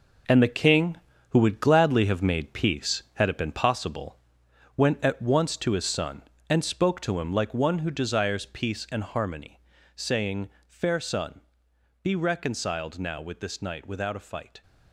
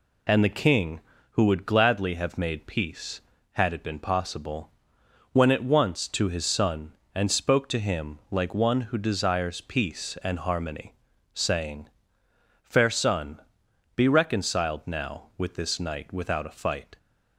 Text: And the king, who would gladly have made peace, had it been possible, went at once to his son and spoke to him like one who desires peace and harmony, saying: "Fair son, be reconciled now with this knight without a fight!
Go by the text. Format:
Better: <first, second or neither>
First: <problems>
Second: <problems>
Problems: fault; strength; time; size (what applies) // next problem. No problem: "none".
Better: second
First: gets quieter; strong; throughout; 9 dB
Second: none